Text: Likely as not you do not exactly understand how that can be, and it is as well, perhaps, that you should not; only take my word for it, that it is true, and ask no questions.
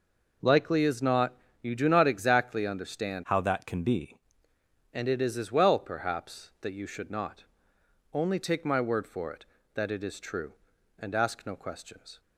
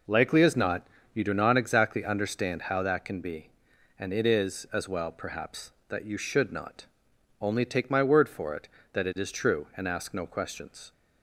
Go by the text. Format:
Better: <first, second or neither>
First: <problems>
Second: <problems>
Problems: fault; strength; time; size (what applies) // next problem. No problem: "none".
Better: second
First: pauses between "not" and "you"; slight; at 1.3 s; 0.26 s long // changes voice from "how" to "be"; from 3.2 to 4.2 s; 1.0 s long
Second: pauses between "not" and "you"; slight; at 0.8 s; 0.26 s long